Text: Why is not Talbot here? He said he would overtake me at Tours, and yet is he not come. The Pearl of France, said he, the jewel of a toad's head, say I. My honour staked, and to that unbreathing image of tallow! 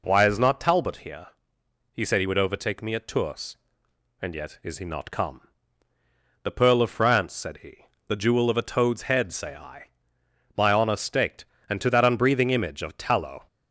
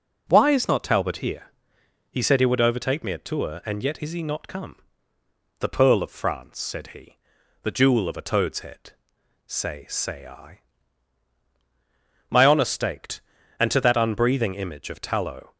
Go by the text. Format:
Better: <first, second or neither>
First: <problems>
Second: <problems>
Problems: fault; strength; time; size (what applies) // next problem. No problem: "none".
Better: first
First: none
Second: says "say" twice; at 9.8 s